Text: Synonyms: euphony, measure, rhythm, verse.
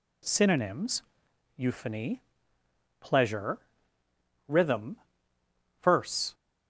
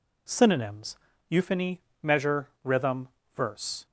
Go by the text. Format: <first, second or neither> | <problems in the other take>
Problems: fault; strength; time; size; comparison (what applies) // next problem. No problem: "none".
second | says "pleasure" for "measure"; at 3.0 s